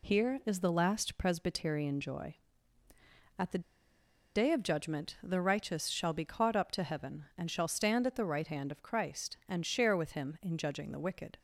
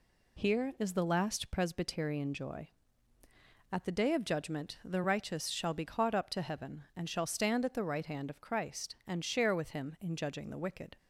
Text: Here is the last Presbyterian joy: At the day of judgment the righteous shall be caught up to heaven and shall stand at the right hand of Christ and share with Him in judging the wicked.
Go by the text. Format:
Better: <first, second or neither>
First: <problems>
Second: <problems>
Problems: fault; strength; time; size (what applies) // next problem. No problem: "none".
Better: second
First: pauses between "the" and "day"; noticeable; at 3.6 s; 0.72 s long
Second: none